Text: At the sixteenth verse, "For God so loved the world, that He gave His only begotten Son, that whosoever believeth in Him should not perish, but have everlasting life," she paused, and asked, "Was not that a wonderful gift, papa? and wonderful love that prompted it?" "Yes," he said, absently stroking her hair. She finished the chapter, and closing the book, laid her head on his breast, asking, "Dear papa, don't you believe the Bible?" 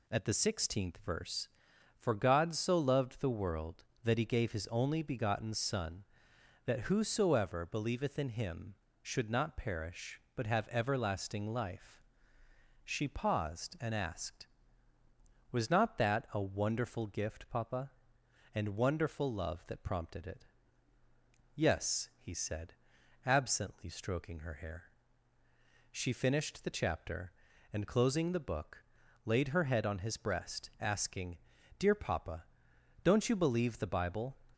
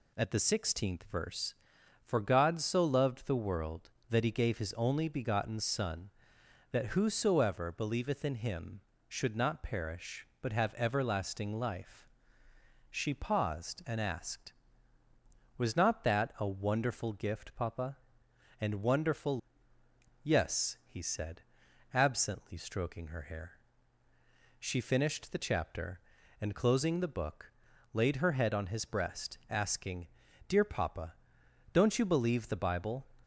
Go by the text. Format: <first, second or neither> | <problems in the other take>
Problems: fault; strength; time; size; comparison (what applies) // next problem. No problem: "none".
first | skips "love that prompted it"; at 19.7 s